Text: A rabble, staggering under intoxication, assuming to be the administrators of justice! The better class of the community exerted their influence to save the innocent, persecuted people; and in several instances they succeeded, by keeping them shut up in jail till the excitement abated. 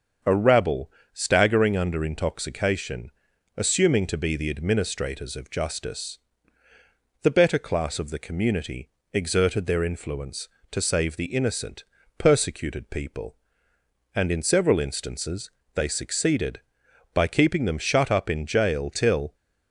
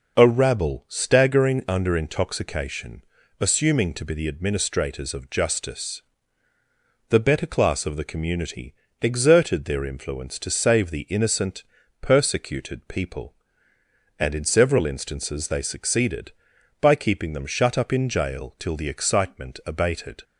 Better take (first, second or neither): second